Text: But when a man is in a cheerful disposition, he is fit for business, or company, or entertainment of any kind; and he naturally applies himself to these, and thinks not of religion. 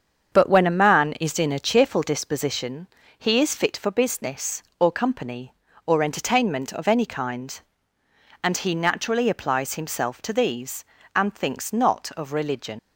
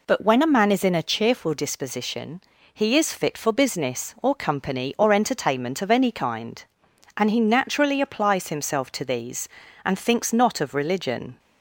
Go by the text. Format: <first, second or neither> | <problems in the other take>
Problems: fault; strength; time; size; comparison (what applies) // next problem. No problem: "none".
second | starts louder than the rest; until 1.4 s; 7 dB // leaves "religion" unfinished; at 12.7 s; 95 ms